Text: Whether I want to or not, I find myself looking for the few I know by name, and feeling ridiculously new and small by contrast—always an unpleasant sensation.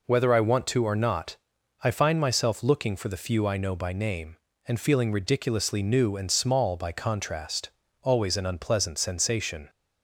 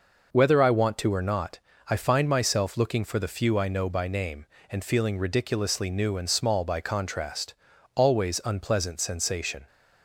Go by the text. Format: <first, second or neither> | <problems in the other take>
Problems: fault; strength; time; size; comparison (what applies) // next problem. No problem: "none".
first | skips "an"; at 8.4 s